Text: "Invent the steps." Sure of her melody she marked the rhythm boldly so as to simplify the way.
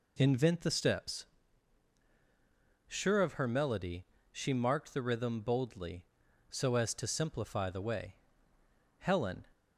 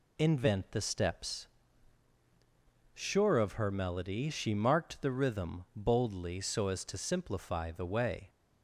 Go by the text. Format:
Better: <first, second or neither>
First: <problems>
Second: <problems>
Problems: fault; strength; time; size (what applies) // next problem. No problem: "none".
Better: second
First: pauses between "melody" and "she"; slight; at 4.0 s; 0.28 s long // goes on to say "Helen"; slight; from 8.9 s on; 0.48 s long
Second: none